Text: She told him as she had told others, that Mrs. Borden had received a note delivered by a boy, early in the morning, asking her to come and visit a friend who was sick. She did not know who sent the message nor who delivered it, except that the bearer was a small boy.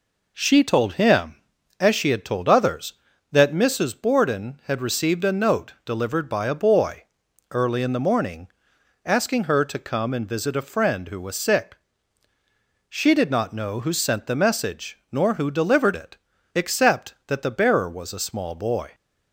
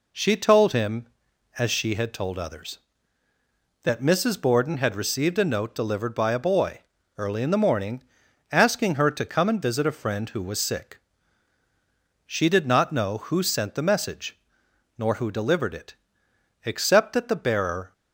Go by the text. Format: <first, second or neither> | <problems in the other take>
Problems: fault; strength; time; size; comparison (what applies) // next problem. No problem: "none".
first | pauses between "message" and "nor"; noticeable; at 14.3 s; 0.62 s long // stops before "was a small boy"; at 17.9 s